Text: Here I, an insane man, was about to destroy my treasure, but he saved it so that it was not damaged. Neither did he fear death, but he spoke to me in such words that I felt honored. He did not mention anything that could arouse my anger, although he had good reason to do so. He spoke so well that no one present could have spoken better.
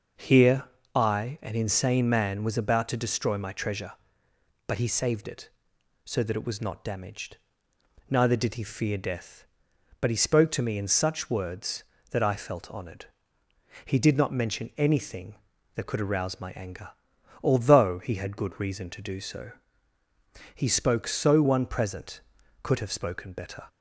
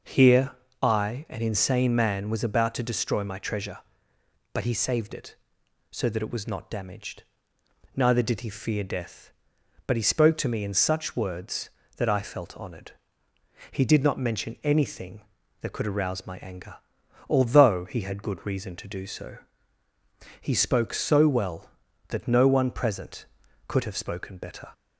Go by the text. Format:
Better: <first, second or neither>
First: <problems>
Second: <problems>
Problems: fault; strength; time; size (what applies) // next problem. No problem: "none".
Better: second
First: pauses between "Here" and "I"; slight; at 0.6 s; 0.30 s long // skips "well that no"; at 21.4 s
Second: pauses between "Here" and "I"; slight; at 0.5 s; 0.30 s long